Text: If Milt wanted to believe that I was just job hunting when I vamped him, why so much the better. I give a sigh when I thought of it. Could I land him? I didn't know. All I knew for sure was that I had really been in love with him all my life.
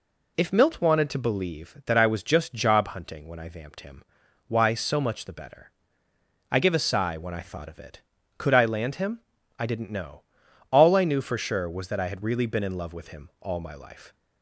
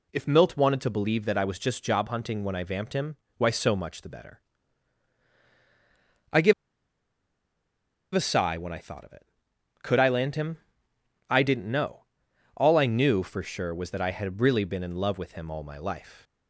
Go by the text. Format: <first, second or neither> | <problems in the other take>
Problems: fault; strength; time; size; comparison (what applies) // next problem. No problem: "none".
first | pauses between "give" and "a"; strong; at 6.5 s; 1.6 s long